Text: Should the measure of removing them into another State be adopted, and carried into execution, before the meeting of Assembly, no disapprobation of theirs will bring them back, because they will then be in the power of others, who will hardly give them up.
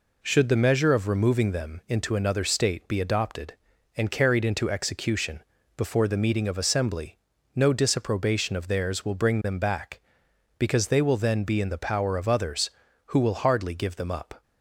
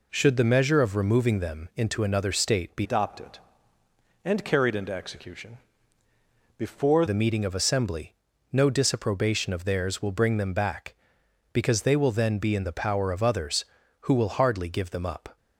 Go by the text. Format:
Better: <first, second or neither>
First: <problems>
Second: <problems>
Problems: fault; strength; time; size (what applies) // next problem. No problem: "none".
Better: first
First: none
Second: changes voice from "adopted" to "before"; from 2.8 to 7.0 s; 4.2 s long